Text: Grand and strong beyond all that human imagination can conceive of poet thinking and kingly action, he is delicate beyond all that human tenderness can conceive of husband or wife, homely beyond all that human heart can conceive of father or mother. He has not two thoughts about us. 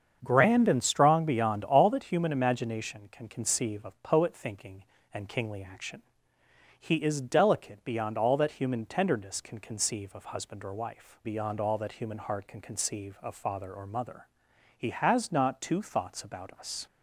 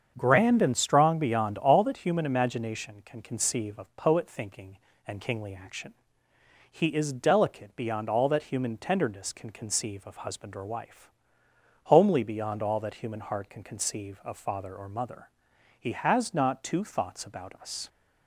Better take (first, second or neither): second